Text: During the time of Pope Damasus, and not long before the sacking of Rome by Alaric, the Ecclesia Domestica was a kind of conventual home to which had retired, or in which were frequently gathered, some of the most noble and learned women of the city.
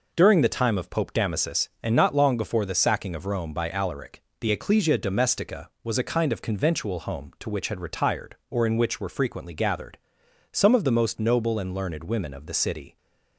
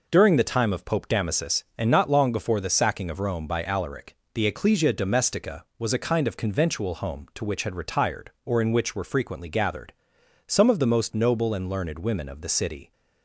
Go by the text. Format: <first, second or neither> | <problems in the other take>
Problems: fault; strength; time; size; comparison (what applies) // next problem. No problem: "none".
neither | none